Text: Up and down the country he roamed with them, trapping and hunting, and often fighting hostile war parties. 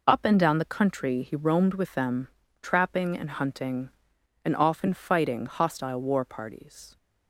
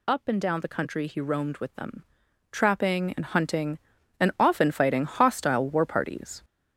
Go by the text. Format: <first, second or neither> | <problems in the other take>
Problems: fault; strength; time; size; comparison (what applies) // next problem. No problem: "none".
first | gets louder; noticeable; throughout; 5.5 dB